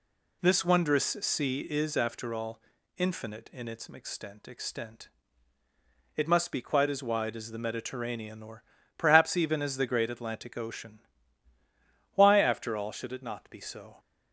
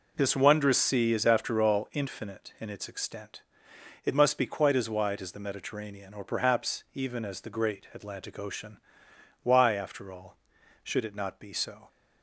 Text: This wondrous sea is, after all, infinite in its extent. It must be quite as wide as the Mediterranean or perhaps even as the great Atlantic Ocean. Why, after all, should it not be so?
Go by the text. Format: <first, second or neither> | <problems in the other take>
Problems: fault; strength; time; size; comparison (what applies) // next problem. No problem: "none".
second | says "extent" twice; at 4.4 s // pauses between "or" and "perhaps"; slight; at 8.6 s; 0.32 s long